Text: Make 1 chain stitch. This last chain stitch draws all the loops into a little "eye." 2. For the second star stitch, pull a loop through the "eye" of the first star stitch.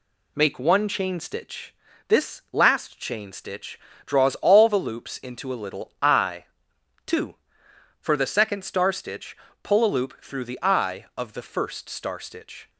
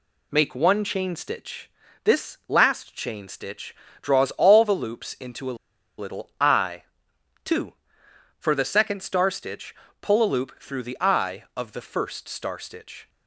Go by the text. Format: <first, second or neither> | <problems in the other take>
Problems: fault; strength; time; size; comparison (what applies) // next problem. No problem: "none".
first | pauses between "stitch" and "draws"; slight; at 3.7 s; 0.26 s long; slight in the first // pauses between "a" and "little"; at 5.5 s; 0.43 s long